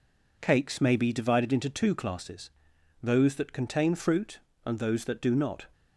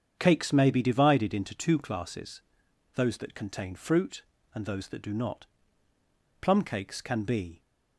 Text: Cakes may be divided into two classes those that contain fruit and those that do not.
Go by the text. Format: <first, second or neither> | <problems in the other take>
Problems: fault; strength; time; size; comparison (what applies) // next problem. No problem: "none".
first | starts louder than the rest; strong; until 1.1 s; 7.5 dB // pauses between "classes" and "those"; noticeable; at 2.4 s; 0.54 s long; noticeable in the first // goes on to say "Plum cakes can be"; noticeable; from 6.4 s on; 1.2 s long